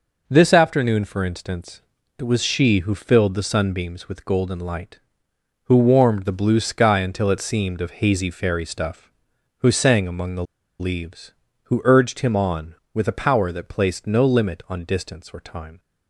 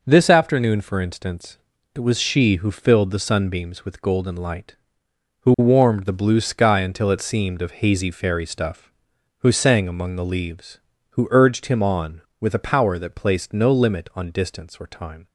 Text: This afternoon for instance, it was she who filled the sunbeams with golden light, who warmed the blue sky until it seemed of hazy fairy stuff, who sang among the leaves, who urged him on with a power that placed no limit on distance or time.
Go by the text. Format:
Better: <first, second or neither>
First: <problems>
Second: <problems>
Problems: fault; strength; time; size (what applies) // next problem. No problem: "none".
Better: second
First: pauses between "the" and "leaves"; at 10.4 s; 0.36 s long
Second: none